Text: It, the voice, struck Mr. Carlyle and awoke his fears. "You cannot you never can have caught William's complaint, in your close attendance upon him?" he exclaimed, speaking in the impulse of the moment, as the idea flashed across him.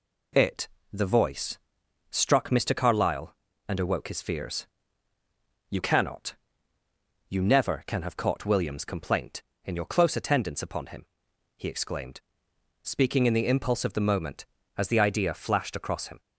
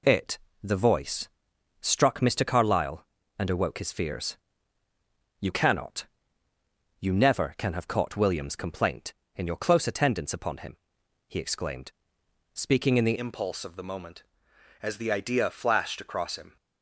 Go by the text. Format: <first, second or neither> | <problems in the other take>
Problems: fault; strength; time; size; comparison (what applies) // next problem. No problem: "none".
first | pauses between "cannot" and "you"; noticeable; at 6.0 s; 0.96 s long; noticeable in the first // changes voice at "impulse"; from 13.1 s on; 3.4 s long